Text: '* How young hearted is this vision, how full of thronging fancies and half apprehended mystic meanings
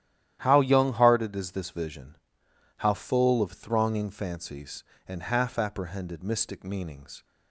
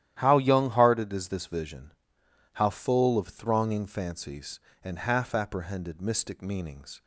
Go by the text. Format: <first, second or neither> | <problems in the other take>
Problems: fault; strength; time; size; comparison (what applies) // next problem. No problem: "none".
neither | starts louder than the rest; strong; the same in both